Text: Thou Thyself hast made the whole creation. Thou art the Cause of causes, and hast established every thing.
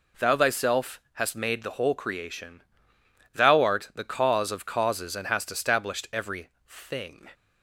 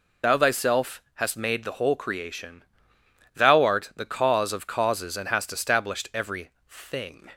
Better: first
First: pauses between "every" and "thing"; slight; at 6.4 s; 0.20 s long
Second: loses the start of "Thou"; at 0.2 s; 60 ms // pauses between "every" and "thing"; slight; at 6.4 s; 0.20 s long

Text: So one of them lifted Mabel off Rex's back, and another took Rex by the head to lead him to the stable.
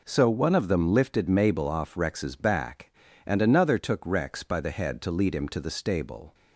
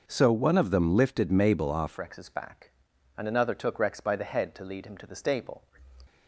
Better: first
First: none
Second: changes voice at "Rex's"; from 1.9 s on; 3.7 s long

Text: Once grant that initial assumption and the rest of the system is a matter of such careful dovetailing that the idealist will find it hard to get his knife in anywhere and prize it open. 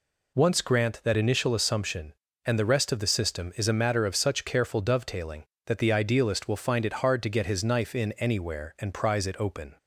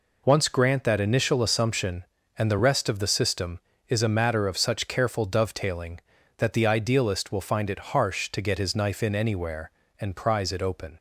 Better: first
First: none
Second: says "harsh" for "hard"; at 7.9 s

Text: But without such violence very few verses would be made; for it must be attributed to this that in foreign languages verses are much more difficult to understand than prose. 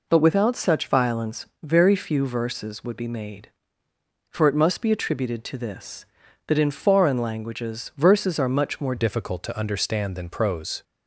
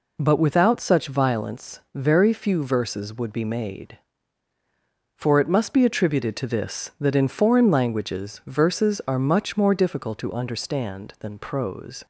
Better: second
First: changes voice at "difficult"; from 8.9 s on; 1.9 s long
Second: none

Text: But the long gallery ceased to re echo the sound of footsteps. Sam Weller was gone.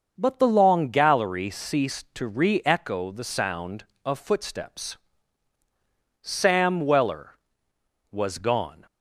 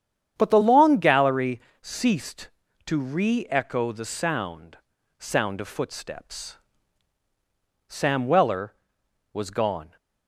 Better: first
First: starts louder than the rest; until 1.1 s; 6.5 dB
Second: starts louder than the rest; strong; until 1.3 s; 9 dB // pauses between "gallery" and "ceased"; slight; at 1.5 s; 0.22 s long // says "sound" twice; at 5.1 s

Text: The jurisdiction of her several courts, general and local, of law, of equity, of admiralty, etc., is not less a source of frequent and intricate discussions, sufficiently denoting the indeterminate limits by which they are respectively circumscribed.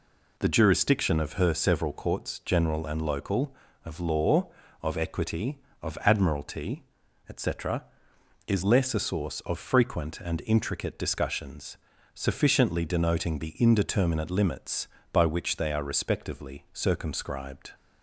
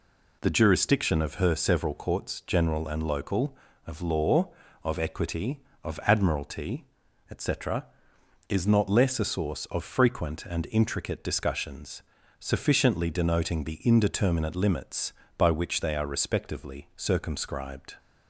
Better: second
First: skips "not"; at 8.6 s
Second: none

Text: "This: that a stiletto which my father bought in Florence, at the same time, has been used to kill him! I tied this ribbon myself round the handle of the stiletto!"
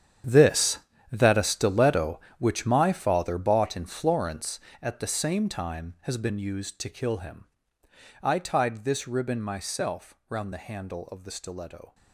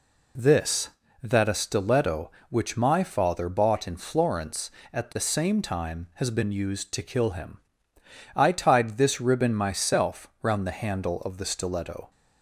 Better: second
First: gets quieter; strong; throughout; 14.5 dB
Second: none

